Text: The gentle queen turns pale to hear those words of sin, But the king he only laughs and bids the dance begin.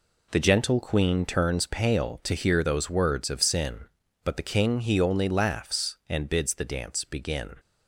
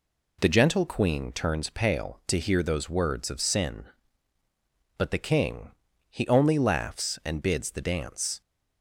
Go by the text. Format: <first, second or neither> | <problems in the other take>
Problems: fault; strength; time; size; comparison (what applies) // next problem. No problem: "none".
first | pauses between "king" and "he"; at 5.7 s; 0.38 s long // stops before "begin"; at 8.4 s